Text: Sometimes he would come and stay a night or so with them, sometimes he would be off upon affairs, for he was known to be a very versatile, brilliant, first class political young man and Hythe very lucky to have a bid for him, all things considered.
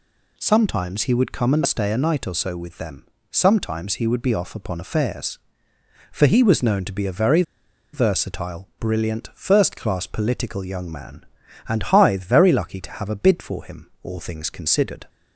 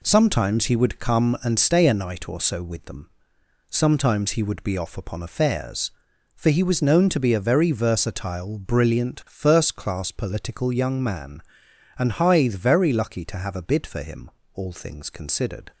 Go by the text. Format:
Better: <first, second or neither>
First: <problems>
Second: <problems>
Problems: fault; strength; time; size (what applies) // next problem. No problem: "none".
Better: second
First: pauses between "very" and "versatile"; noticeable; at 7.4 s; 0.51 s long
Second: none